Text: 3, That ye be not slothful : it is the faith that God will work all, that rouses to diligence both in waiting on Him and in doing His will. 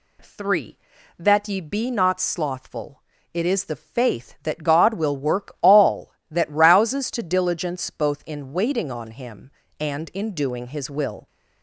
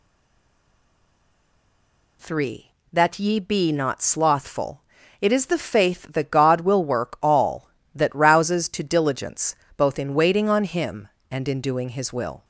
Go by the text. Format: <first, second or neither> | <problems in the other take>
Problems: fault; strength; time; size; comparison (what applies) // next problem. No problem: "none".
first | stays silent before the first word; until 2.2 s; 2.2 s long // pauses between "diligence" and "both"; slight; at 9.5 s; 0.24 s long